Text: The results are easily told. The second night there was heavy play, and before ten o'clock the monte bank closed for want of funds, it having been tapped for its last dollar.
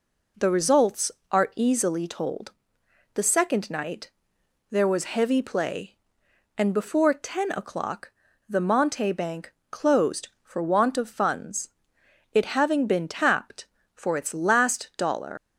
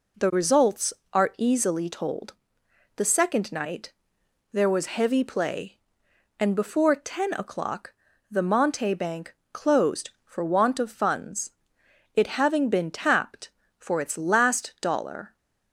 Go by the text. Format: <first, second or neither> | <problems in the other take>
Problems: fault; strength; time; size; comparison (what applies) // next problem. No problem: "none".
second | pauses between "night" and "there"; noticeable; at 4.1 s; 0.58 s long; noticeable in the second // pauses between "o'clock" and "the"; at 8.1 s; 0.38 s long; also in the second // pauses between "bank" and "closed"; slight; at 9.5 s; 0.18 s long; slight in the second // leaves "dollar" unfinished; at 15.3 s; 150 ms